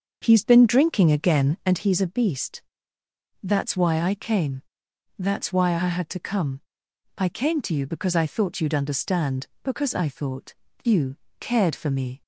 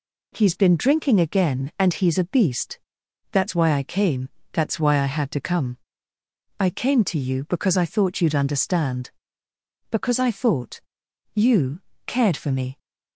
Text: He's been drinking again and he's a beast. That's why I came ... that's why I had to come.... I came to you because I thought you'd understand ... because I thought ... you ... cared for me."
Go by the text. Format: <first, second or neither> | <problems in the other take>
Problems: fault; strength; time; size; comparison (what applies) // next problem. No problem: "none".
second | starts louder than the rest; until 1.8 s; 6.5 dB